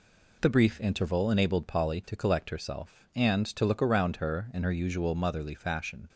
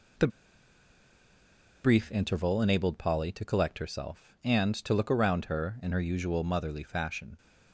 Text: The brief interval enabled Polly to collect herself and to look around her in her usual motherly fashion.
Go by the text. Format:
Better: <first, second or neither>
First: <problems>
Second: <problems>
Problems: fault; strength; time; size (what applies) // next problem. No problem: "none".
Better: first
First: none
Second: pauses between "The" and "brief"; strong; at 0.2 s; 1.5 s long